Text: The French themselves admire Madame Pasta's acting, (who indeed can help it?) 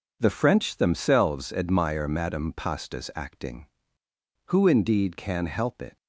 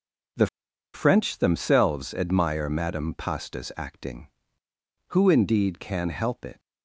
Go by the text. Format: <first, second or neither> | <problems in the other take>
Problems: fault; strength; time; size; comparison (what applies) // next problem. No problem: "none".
first | pauses between "The" and "French"; noticeable; at 0.4 s; 0.47 s long